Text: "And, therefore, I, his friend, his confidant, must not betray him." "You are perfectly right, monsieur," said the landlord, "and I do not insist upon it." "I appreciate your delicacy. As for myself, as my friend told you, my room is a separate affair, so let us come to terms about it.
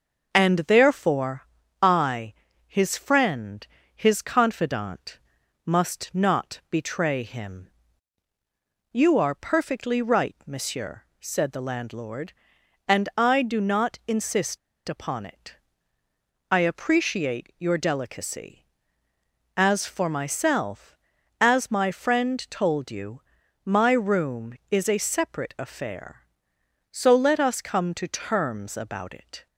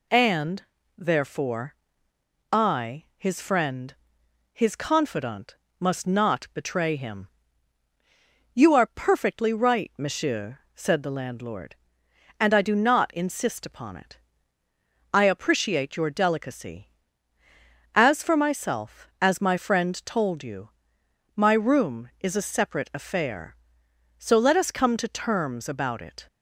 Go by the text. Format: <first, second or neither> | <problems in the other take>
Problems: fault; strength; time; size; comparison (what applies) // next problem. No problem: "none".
second | pauses between "insist" and "upon"; slight; at 14.5 s; 0.29 s long